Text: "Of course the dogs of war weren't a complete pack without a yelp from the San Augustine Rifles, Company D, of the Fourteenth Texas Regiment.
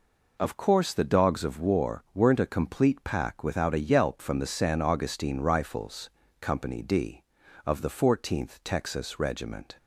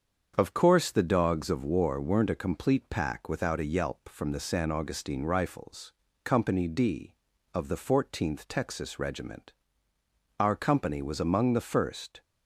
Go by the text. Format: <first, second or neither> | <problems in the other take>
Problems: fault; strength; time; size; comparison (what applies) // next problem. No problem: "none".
first | starts louder than the rest; strong; until 1.3 s; 7 dB // goes on to say "Our company was among the first"; strong; from 10.4 s on; 1.8 s long